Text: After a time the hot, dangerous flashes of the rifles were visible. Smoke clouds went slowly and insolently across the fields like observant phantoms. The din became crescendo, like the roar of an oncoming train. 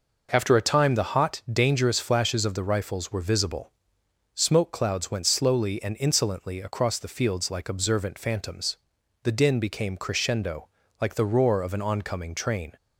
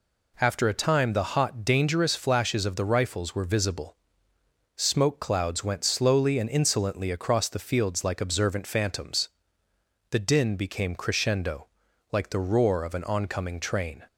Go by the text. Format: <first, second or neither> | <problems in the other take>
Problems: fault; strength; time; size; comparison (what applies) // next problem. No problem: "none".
neither | none